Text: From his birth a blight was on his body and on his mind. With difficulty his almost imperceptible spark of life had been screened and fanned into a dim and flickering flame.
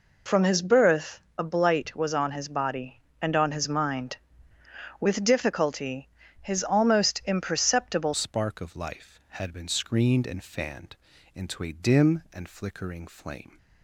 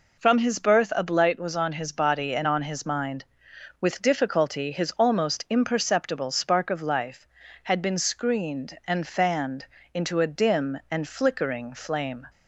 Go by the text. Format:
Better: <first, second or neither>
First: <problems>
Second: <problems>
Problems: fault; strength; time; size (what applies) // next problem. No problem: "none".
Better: second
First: pauses between "birth" and "a"; slight; at 1.2 s; 0.18 s long // pauses between "difficulty" and "his"; slight; at 6.0 s; 0.32 s long // changes voice at "spark"; from 8.1 s on; 5.4 s long // pauses between "fanned" and "into"; at 10.9 s; 0.38 s long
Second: pauses between "fanned" and "into"; slight; at 9.6 s; 0.26 s long